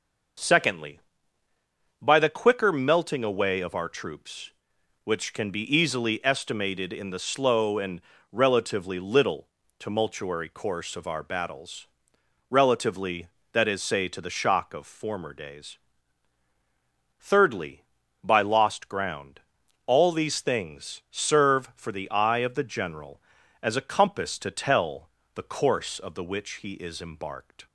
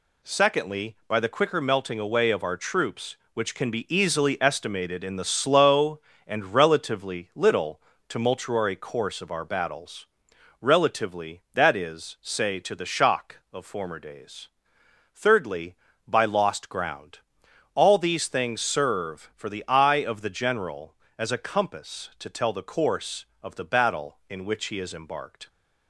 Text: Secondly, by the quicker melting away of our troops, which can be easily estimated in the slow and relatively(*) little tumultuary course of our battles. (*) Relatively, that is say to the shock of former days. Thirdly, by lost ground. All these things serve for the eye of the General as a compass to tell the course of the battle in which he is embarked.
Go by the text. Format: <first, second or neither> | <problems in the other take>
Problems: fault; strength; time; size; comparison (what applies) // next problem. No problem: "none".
second | pauses between "and" and "relatively"; slight; at 8.0 s; 0.30 s long // pauses between "little" and "tumultuary"; slight; at 9.4 s; 0.32 s long; slight in the second // pauses between "tell" and "the"; slight; at 25.0 s; 0.26 s long // skips "battle in"; at 26.2 s